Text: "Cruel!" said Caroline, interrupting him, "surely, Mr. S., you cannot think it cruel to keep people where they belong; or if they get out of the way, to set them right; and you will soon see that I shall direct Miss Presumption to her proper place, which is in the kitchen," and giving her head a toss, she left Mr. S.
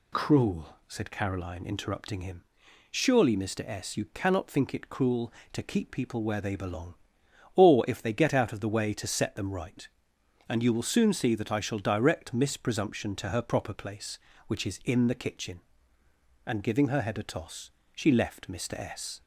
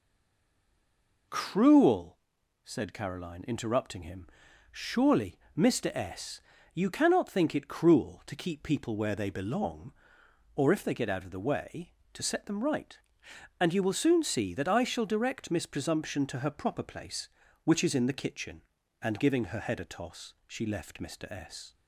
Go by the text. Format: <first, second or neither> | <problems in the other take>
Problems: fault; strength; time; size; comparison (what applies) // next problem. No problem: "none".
first | stays silent before the first word; noticeable; until 1.2 s; 1.2 s long